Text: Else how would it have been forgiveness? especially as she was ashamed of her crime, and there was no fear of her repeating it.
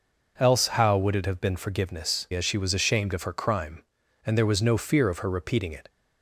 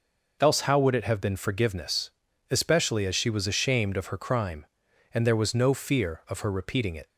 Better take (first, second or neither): second